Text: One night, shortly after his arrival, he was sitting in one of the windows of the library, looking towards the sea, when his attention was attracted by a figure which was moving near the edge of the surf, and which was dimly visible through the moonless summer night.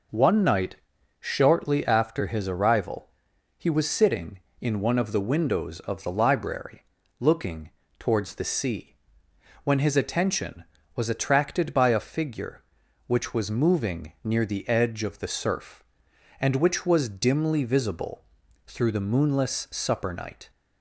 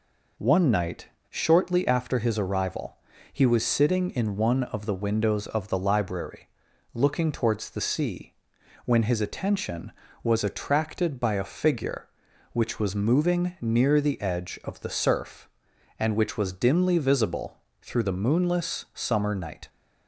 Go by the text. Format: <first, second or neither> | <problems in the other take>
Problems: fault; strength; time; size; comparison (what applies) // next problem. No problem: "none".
second | pauses between "looking" and "towards"; slight; at 7.7 s; 0.28 s long // pauses between "visible" and "through"; noticeable; at 18.2 s; 0.46 s long; slight in the second // says "supper" for "summer"; at 19.7 s